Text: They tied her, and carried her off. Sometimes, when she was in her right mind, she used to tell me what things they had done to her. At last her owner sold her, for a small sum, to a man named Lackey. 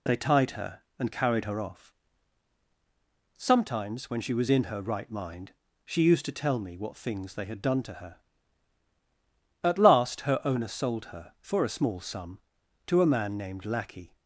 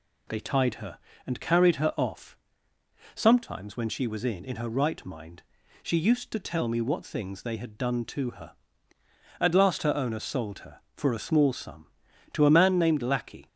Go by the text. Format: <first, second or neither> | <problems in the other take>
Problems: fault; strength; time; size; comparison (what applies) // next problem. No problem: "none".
first | says "in" twice; at 4.4 s